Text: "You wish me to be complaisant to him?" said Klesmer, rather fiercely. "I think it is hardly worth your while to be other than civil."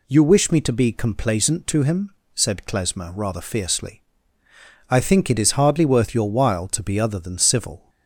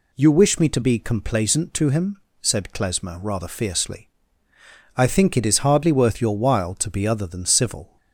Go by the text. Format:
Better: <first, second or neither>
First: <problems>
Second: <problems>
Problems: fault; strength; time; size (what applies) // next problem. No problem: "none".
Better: neither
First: none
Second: none